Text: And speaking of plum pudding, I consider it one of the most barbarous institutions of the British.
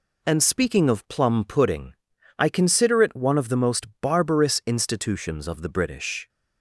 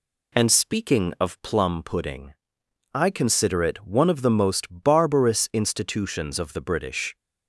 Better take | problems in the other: neither | none

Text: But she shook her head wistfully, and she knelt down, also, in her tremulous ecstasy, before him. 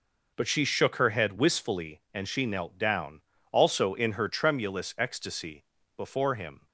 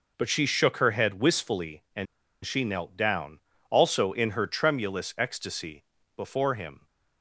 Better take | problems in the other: first | pauses between "and" and "she"; at 2.0 s; 0.38 s long

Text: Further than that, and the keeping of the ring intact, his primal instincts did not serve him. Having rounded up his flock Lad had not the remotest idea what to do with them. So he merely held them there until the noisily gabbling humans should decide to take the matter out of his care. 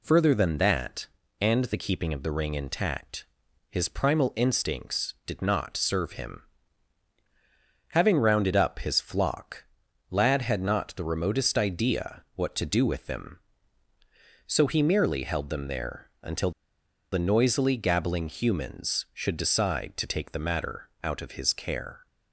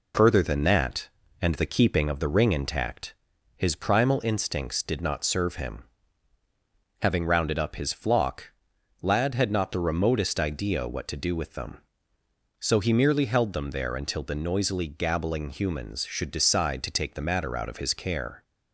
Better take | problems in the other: second | pauses between "flock" and "Lad"; noticeable; at 9.6 s; 0.48 s long; noticeable in the second // pauses between "until" and "the"; noticeable; at 16.5 s; 0.61 s long // pauses between "matter" and "out"; slight; at 20.8 s; 0.16 s long

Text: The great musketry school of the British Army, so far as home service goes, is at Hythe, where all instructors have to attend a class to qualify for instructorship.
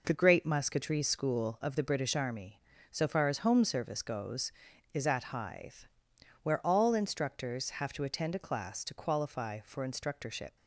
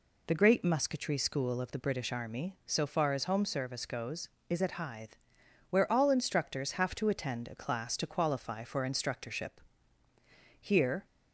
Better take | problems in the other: first | goes on to say "Here"; slight; from 10.5 s on; 0.46 s long

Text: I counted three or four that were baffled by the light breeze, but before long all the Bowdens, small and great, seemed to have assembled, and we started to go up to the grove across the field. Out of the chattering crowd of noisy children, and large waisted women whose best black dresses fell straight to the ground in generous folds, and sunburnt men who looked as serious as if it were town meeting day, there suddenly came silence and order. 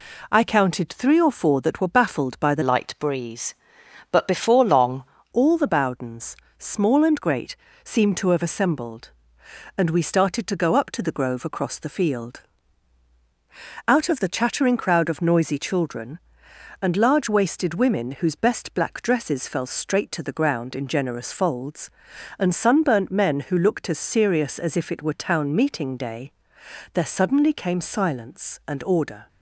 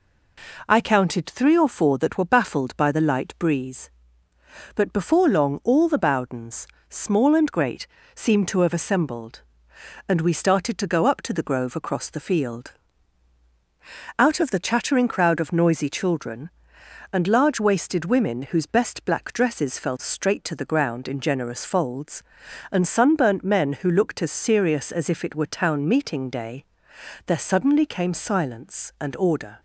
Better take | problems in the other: second | changes voice from "light" to "long"; from 2.6 to 5.0 s; 2.4 s long

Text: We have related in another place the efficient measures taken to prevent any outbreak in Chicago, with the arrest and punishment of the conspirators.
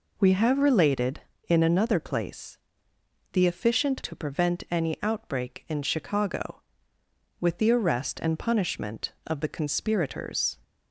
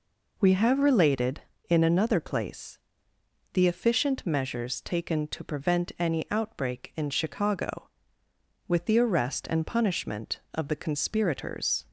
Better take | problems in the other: second | pauses between "place" and "the"; noticeable; at 2.5 s; 0.76 s long; noticeable in the second // skips "measures taken"; at 4.0 s

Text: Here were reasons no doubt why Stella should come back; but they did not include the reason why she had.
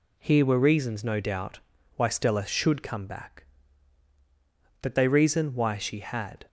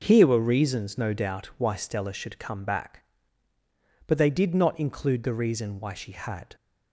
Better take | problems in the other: second | pauses between "doubt" and "why"; slight; at 1.6 s; 0.34 s long // skips "did not include the"; at 5.0 s

